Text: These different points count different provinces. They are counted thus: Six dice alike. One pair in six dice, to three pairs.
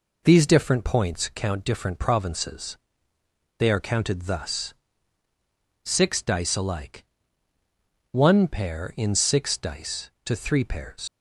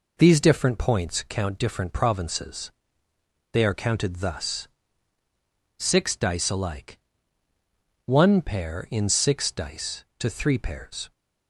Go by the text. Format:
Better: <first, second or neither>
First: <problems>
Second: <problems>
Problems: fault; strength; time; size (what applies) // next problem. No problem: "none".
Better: second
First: leaves "pairs" unfinished; at 11.0 s; 95 ms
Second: none